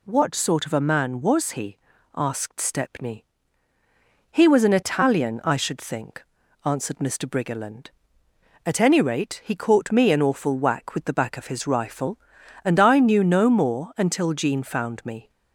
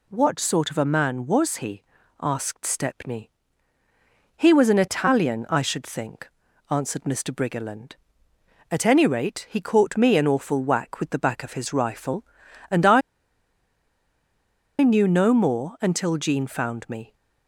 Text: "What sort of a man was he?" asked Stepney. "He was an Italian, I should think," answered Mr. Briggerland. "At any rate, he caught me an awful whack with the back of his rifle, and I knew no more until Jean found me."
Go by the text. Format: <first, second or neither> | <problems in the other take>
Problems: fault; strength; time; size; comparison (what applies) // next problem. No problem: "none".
first | pauses between "I" and "knew"; strong; at 13.0 s; 1.8 s long